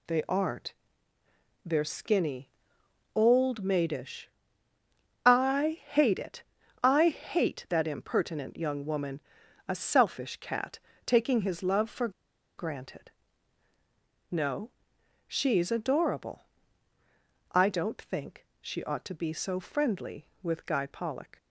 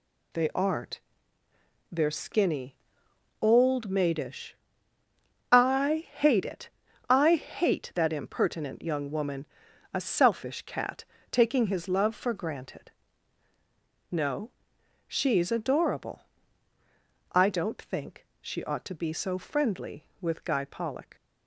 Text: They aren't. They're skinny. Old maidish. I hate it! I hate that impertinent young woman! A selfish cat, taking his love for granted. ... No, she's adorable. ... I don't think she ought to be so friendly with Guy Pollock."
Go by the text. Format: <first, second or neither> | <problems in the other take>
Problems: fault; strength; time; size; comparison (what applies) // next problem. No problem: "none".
second | pauses between "for" and "granted"; noticeable; at 12.0 s; 0.48 s long